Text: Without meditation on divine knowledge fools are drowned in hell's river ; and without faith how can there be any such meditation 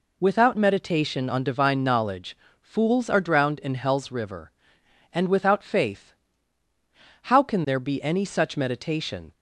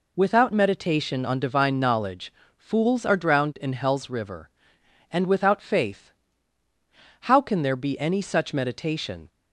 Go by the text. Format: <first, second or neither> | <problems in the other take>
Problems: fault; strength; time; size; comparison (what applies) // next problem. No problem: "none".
neither | pauses between "knowledge" and "fools"; slight; the same in both // pauses between "faith" and "how"; the same in both